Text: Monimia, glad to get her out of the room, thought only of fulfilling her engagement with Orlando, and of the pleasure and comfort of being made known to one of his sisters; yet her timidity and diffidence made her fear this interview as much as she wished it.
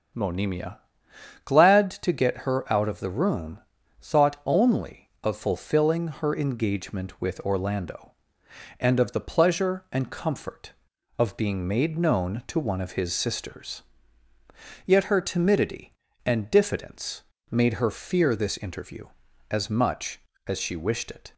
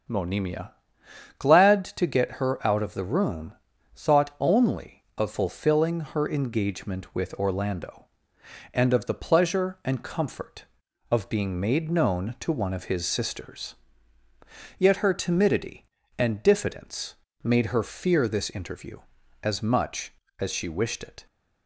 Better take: neither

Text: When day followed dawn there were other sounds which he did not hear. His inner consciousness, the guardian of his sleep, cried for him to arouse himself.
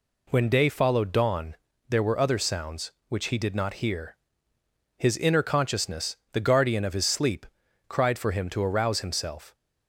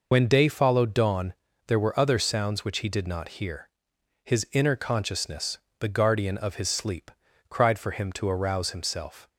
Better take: first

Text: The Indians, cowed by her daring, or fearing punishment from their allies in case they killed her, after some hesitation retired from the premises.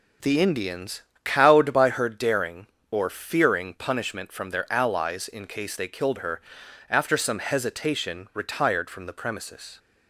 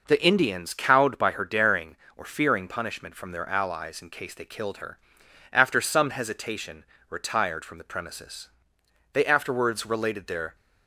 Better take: first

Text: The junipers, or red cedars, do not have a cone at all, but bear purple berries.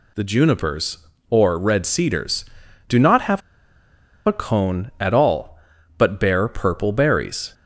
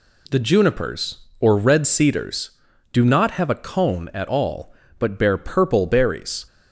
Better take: second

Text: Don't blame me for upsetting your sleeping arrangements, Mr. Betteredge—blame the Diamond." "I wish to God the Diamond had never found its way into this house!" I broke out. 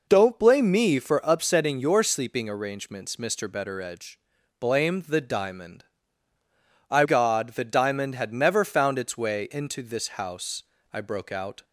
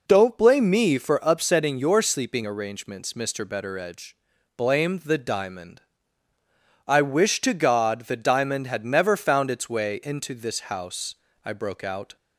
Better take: second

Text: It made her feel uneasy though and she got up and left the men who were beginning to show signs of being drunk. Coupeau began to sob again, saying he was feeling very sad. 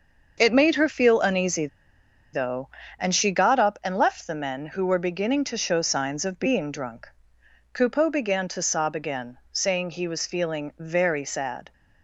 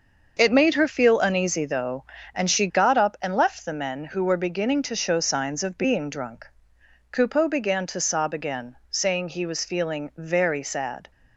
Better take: second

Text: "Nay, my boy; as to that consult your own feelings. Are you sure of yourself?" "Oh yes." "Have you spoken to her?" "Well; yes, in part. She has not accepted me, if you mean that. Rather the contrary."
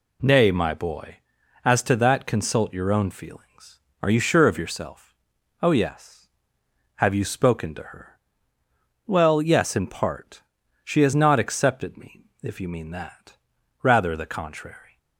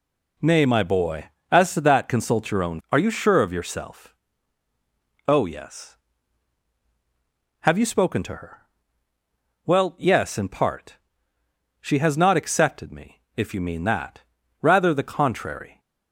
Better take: first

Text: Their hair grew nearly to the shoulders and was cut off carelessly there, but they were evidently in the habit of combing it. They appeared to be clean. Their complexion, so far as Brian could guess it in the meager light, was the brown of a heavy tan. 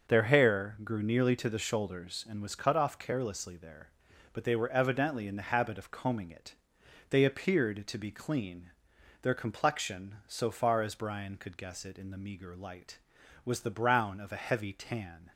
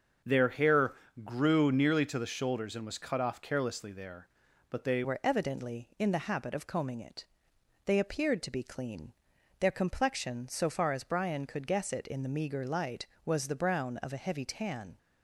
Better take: first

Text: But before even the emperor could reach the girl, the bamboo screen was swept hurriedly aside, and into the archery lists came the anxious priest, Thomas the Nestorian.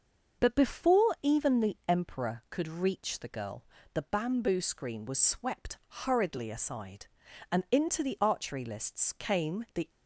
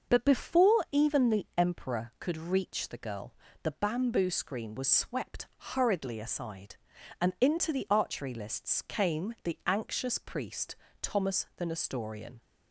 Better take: second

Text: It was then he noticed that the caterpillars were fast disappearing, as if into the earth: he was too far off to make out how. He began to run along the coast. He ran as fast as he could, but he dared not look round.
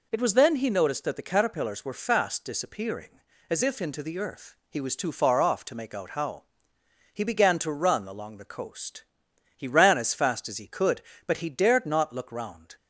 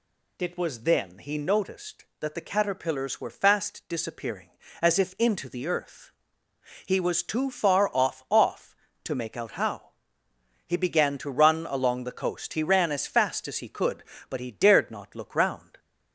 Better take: first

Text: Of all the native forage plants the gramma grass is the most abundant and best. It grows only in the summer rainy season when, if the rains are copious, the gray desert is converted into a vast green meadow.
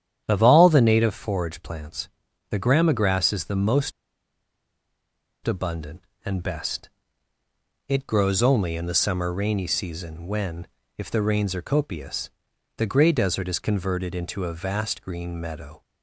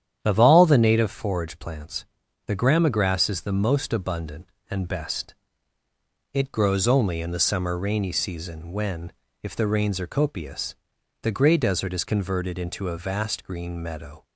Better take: second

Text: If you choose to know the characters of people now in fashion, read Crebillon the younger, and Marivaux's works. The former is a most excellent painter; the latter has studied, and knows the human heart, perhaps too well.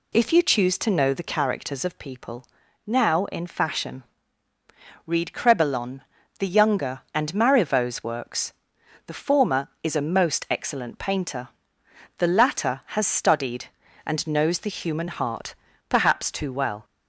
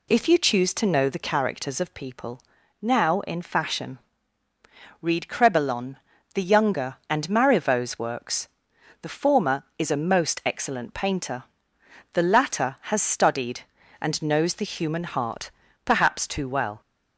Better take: neither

